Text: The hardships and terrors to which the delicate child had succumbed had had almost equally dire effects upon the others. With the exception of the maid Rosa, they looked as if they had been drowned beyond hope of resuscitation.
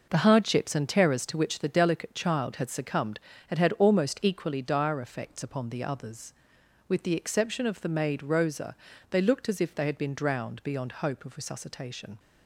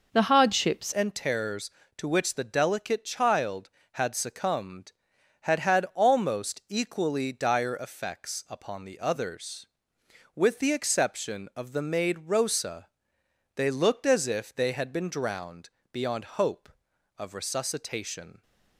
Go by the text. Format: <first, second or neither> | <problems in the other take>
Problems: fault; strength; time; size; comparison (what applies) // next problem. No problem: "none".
first | changes voice at "and"; from 0.9 s on; 17.5 s long // pauses between "drowned" and "beyond"; slight; at 15.6 s; 0.22 s long